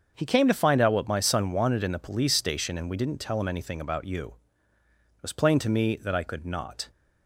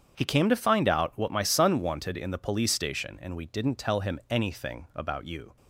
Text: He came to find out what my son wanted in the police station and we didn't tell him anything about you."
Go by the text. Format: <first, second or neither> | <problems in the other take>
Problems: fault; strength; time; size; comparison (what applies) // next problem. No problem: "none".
second | starts louder than the rest; until 1.1 s; 7 dB; strong in the second // goes on to say "It was plain to me that I could not"; strong; from 5.1 s on; 1.7 s long